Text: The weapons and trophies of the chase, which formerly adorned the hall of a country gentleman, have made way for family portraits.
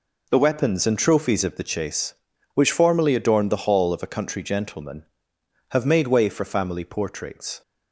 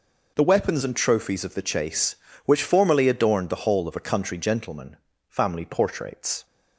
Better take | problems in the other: first | skips "have made way for"; at 5.1 s

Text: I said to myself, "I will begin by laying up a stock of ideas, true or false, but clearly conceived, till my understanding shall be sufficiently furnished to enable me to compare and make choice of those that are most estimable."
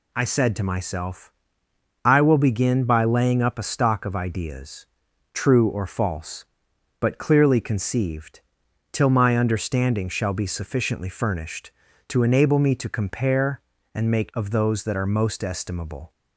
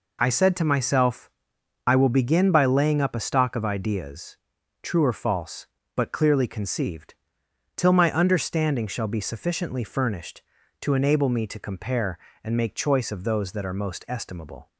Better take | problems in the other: second | skips "choice"; at 14.3 s

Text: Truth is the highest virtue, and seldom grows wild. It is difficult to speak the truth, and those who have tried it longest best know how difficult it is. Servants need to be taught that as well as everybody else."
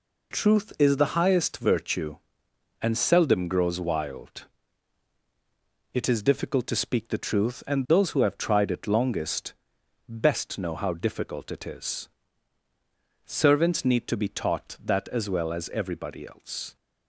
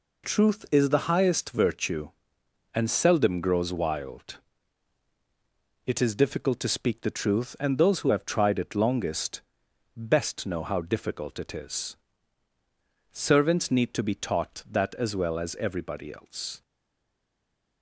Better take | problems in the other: first | pauses between "longest" and "best"; noticeable; at 9.4 s; 0.56 s long; noticeable in the first // stays silent after the last word; noticeable; from 16.6 s on; 1.2 s long

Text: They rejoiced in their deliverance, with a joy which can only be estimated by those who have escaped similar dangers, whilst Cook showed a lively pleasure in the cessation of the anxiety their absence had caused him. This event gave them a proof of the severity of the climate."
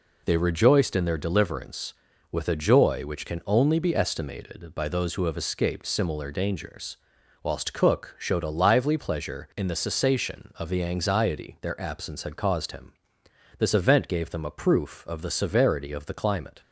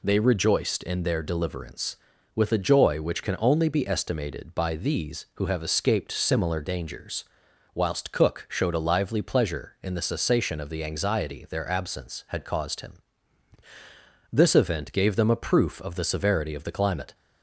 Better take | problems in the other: first | says "these" for "those"; at 4.7 s

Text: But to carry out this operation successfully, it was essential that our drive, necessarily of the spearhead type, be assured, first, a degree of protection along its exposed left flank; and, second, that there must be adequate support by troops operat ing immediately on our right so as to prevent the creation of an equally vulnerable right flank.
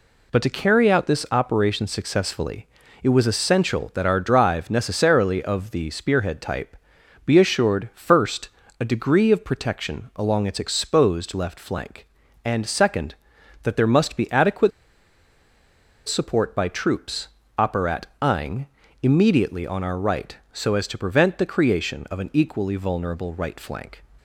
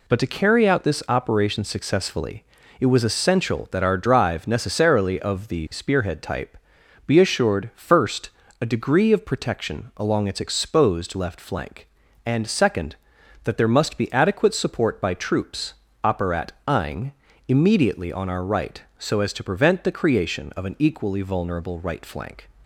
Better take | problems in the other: second | pauses between "adequate" and "support"; strong; at 14.7 s; 1.3 s long // pauses between "troops" and "operat"; slight; at 17.2 s; 0.28 s long; slight in the second // pauses between "operat" and "ing"; slight; at 18.0 s; 0.16 s long; slight in the second // pauses between "ing" and "immediately"; slight; at 18.6 s; 0.34 s long; slight in the second

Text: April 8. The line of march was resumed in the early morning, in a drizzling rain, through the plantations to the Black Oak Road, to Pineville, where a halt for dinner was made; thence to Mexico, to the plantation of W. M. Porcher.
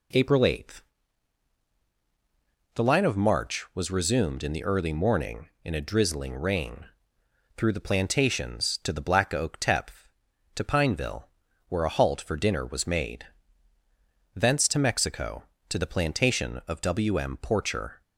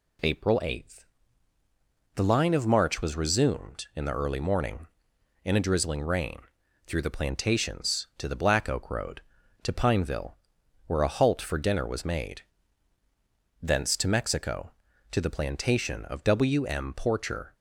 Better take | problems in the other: second | says "Tepth" for "Road"; at 9.5 s

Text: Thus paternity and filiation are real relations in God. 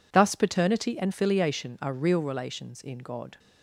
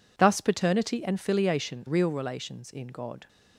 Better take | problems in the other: first | skips "are"; at 1.8 s

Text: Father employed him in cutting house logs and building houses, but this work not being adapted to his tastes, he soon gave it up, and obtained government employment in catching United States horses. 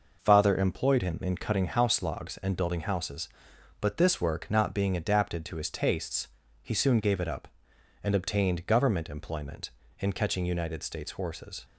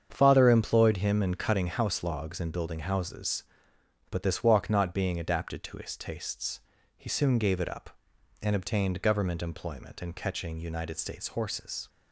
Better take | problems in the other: first | starts louder than the rest; strong; until 1.1 s; 7.5 dB // says "walk" for "work"; at 4.4 s

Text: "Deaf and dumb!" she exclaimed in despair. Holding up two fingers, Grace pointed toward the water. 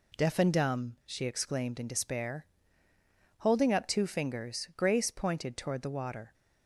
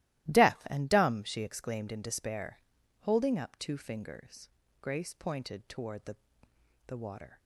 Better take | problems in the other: first | starts louder than the rest; strong; until 1.3 s; 16 dB // says "the" twice; at 6.8 s

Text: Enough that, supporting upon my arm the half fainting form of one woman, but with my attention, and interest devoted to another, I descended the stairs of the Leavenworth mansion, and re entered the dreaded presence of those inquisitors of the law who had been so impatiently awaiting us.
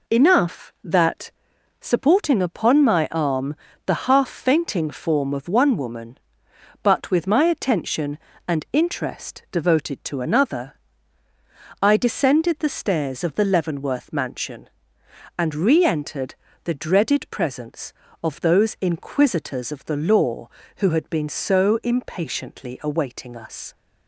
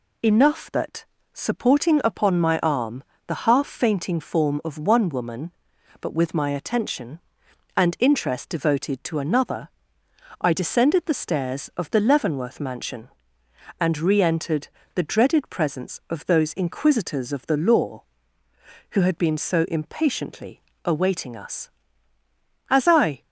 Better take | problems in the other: first | pauses between "arm" and "the"; slight; at 3.0 s; 0.24 s long; slight in the first // pauses between "entered" and "the"; slight; at 14.6 s; 0.26 s long; slight in the first // goes on to say "As I"; from 22.7 s on; 0.52 s long

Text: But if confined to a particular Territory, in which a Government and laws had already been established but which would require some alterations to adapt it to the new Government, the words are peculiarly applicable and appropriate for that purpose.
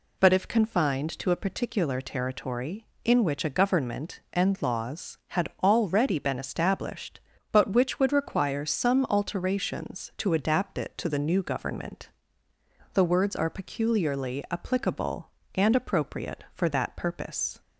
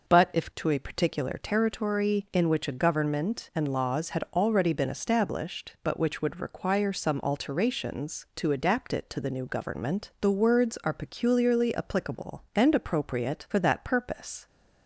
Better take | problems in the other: first | skips "confined"; at 0.5 s

